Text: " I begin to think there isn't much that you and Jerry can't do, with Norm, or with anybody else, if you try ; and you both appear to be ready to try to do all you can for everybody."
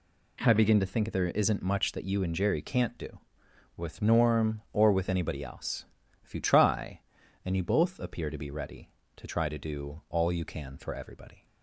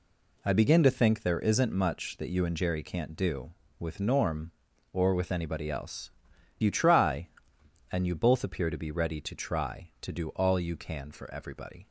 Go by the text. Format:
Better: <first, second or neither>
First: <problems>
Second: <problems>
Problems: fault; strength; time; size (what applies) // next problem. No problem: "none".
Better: first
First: none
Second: skips "if"; at 6.3 s